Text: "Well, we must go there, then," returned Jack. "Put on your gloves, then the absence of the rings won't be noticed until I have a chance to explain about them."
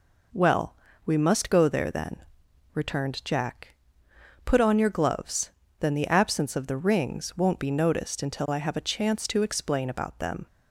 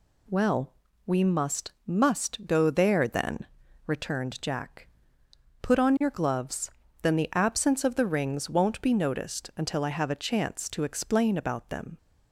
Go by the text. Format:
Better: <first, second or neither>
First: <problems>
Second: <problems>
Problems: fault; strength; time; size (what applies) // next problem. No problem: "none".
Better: first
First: none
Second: says "must" twice; at 1.8 s